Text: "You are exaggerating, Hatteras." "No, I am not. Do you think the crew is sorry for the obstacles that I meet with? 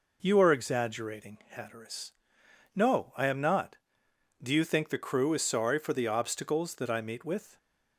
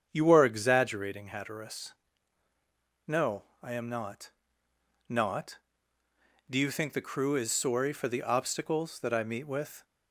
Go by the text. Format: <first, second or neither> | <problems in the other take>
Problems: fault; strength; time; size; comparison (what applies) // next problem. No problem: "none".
first | starts louder than the rest; strong; until 1.1 s; 7.5 dB // says "not" twice; at 5.0 s